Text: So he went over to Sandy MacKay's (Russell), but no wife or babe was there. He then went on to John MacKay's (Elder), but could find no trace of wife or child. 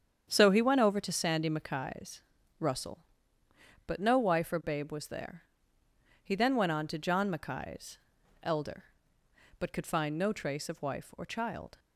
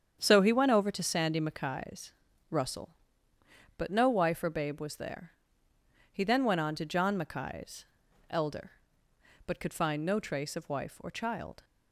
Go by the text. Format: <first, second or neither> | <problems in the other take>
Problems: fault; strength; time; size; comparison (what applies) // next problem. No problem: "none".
neither | starts louder than the rest; strong; the same in both